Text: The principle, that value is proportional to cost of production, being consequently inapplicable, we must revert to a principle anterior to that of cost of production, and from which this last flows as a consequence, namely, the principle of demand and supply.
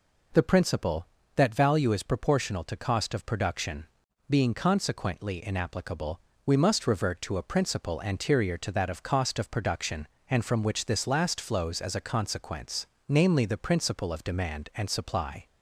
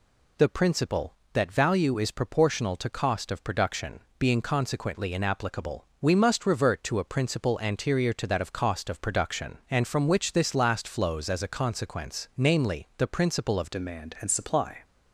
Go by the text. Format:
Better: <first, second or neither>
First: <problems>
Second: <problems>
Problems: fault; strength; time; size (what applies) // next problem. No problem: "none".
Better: first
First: none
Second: changes voice at "demand"; from 13.7 s on; 1.1 s long